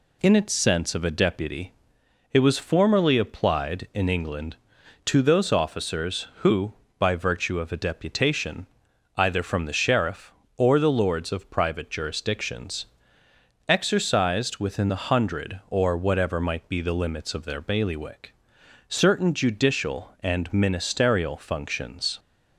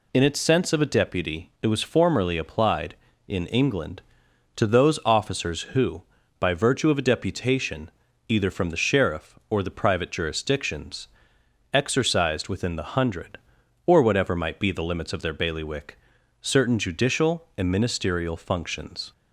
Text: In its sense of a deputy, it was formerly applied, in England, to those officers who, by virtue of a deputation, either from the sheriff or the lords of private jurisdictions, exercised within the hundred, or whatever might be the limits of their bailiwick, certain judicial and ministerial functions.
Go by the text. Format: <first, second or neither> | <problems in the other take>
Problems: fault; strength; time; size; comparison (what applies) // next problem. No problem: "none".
first | skips "lords of"; at 9.6 s